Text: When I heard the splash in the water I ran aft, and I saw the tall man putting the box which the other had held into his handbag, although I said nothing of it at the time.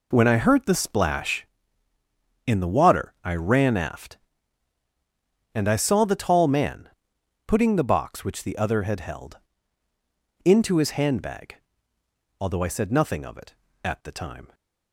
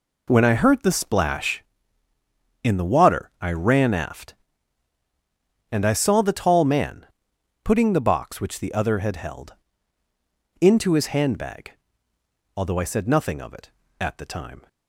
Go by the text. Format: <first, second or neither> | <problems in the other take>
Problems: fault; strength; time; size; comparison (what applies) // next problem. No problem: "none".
neither | pauses between "man" and "putting"; noticeable; the same in both // pauses between "held" and "into"; the same in both